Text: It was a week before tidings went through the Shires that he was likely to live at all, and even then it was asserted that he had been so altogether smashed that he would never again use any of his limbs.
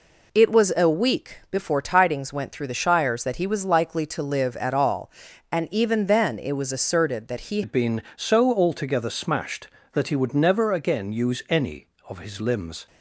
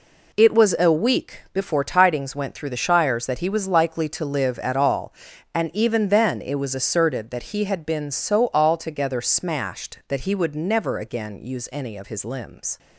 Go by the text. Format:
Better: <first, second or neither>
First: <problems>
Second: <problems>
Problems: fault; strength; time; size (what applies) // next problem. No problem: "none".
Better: second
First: changes voice at "had"; from 7.6 s on; 5.2 s long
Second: none